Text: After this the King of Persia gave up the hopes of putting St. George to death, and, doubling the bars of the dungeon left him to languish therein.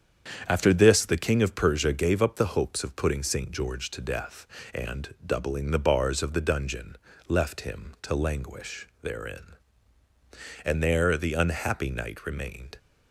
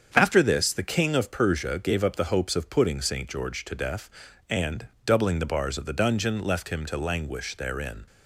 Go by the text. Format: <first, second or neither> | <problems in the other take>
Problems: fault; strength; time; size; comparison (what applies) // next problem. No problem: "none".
second | starts louder than the rest; strong; until 1.5 s; 8 dB; strong in the second // pauses between "dungeon" and "left"; slight; at 6.9 s; 0.32 s long // goes on to say "And there the unhappy Knight remained"; strong; from 10.6 s on; 2.1 s long